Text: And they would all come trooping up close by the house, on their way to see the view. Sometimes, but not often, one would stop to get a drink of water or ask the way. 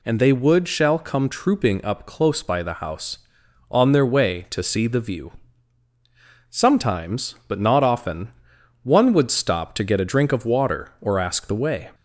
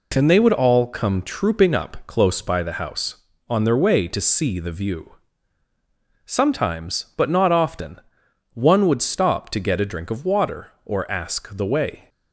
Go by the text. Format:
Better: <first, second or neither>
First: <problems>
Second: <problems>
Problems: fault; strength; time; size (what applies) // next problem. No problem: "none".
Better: second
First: says "shall" for "all"; at 0.6 s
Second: none